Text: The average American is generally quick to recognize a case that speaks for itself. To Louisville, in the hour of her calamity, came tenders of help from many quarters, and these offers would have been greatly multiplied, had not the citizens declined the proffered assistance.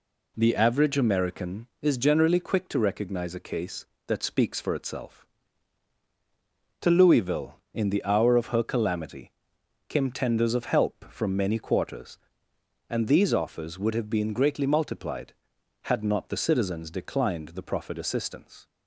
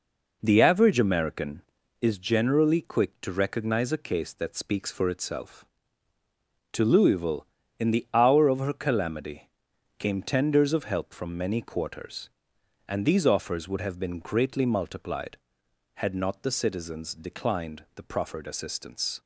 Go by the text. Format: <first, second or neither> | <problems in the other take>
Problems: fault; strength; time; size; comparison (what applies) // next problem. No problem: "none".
neither | none